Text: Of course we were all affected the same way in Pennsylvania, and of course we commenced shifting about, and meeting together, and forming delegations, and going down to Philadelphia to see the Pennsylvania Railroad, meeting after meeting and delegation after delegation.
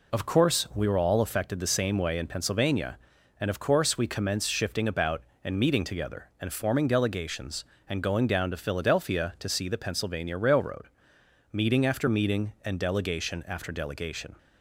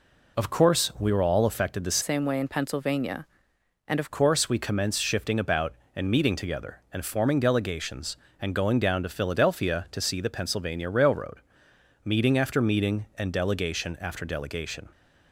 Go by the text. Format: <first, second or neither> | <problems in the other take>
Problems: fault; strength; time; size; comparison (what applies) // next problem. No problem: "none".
first | changes voice from "same" to "of"; from 2.0 to 4.1 s; 2.1 s long